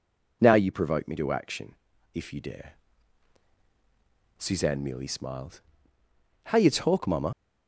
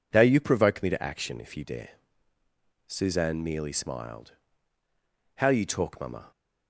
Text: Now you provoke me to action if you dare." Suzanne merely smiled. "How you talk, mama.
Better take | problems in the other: second | pauses between "action" and "if"; at 1.7 s; 0.40 s long // leaves "mama" unfinished; at 7.3 s; 100 ms

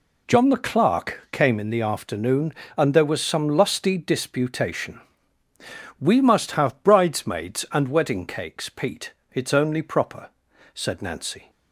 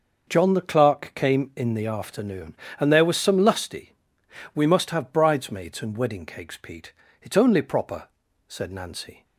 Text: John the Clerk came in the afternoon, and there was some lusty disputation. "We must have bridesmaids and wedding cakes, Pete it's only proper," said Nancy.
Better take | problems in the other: first | skips "disputation"; at 4.2 s // pauses between "Pete" and "it's"; slight; at 6.9 s; 0.30 s long; slight in the first

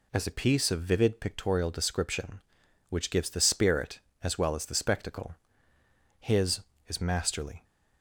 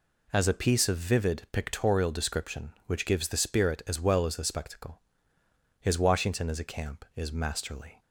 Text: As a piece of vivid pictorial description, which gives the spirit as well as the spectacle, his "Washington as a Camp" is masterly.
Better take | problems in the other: second | skips "Washington as a Camp"; at 6.7 s

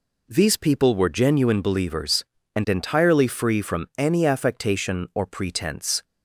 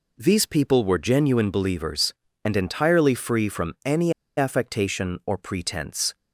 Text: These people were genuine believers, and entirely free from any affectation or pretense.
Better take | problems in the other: first | pauses between "any" and "affectation"; slight; at 4.1 s; 0.25 s long

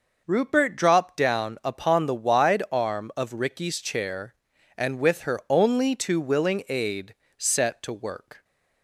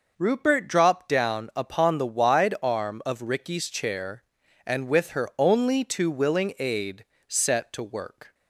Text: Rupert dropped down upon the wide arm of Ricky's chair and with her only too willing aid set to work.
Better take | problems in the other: neither | pauses between "aid" and "set"; slight; the same in both

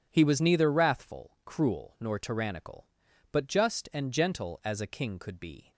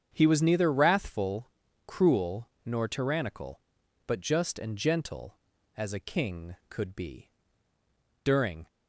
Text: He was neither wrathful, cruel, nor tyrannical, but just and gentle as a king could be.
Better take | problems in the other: first | starts louder than the rest; strong; until 1.1 s; 8 dB // goes on to say "During"; slight; from 8.2 s on; 0.44 s long

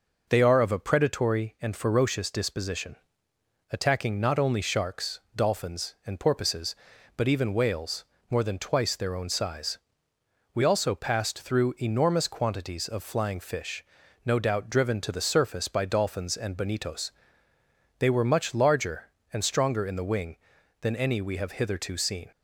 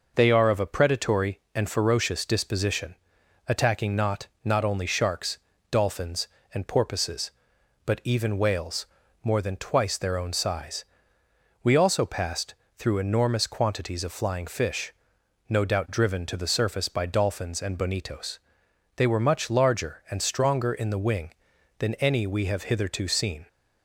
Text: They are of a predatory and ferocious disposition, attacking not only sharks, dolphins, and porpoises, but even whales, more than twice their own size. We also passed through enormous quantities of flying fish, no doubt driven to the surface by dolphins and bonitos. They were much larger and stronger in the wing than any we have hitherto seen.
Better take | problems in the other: first | says "not" twice; at 4.4 s // pauses between "passed" and "through"; slight; at 12.5 s; 0.24 s long

